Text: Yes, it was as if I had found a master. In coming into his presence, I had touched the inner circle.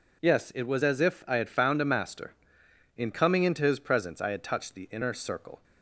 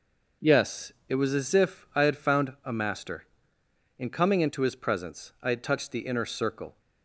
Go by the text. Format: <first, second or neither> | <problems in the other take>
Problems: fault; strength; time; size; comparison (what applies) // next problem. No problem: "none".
neither | none